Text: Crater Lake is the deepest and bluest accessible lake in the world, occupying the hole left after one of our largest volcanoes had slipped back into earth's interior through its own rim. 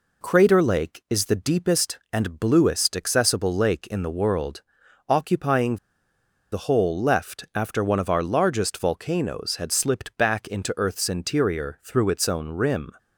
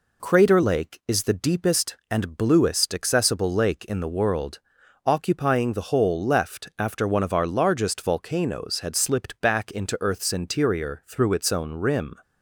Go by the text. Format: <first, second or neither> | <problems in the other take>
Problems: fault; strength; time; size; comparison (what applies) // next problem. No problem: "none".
second | pauses between "occupying" and "the"; noticeable; at 5.7 s; 0.76 s long